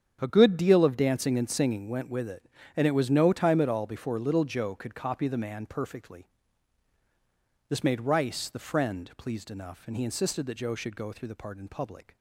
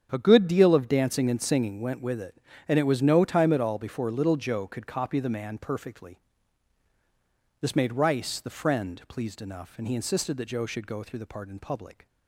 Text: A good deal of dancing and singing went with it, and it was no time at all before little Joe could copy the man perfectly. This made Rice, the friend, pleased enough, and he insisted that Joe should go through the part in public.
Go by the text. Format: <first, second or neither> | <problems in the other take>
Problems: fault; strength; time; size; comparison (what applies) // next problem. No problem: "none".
neither | starts louder than the rest; strong; the same in both